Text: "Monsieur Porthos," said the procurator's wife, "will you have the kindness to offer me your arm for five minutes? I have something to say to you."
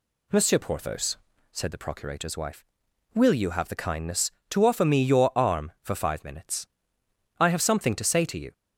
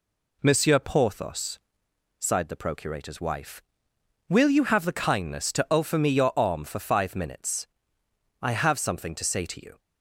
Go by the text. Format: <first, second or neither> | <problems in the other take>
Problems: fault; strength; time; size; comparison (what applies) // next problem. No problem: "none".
first | says "sighed" for "said"; at 2.2 s